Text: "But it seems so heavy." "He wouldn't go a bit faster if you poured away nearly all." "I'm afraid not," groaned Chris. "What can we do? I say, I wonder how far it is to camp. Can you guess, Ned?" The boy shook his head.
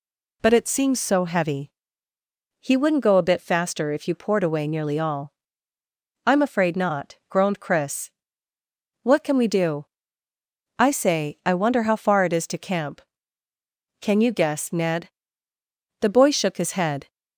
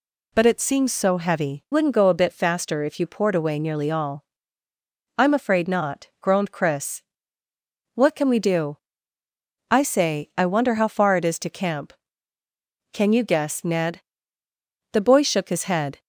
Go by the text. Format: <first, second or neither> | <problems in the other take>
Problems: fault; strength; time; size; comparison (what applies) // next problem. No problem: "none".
first | skips "He"; at 1.6 s